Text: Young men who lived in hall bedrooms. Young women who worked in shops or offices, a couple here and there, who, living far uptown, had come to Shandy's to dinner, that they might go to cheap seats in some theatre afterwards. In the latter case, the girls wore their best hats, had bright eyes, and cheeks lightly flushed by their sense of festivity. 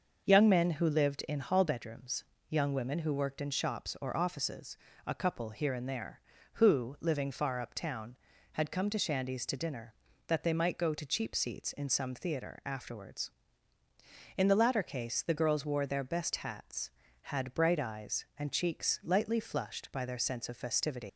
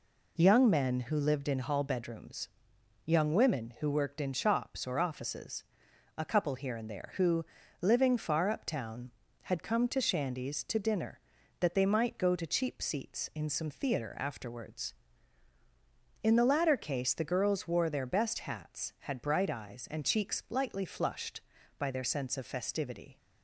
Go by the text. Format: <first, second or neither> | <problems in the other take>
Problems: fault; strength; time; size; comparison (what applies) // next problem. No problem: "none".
second | starts louder than the rest; until 1.3 s; 6 dB // leaves "festivity" unfinished; at 21.0 s; 115 ms